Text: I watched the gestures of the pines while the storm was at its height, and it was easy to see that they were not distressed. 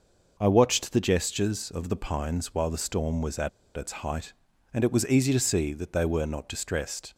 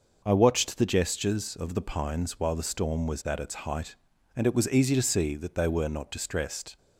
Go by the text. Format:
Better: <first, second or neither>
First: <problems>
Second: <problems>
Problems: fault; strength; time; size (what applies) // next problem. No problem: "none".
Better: second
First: pauses between "at" and "its"; slight; at 3.4 s; 0.26 s long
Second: none